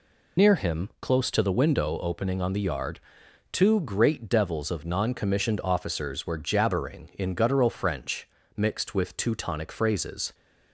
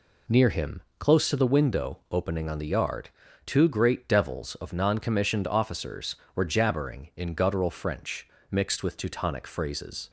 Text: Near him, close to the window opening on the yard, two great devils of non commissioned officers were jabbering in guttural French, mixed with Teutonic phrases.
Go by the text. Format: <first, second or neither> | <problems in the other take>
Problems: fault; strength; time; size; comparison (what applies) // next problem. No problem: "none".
second | loses the start of "Near"; at 0.3 s; 75 ms